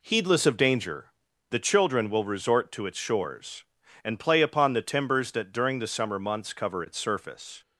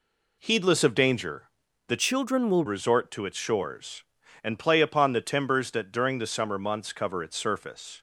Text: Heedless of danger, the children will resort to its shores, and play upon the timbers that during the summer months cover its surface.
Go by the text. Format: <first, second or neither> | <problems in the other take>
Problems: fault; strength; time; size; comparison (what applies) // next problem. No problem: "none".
first | changes voice from "children" to "will"; from 1.9 to 2.6 s; 0.7 s long